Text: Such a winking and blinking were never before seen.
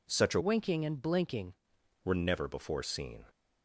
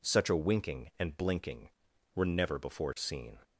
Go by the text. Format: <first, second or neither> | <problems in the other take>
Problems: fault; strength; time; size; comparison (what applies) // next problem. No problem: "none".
second | changes voice from "winking" to "blinking"; from 0.3 to 1.5 s; 1.2 s long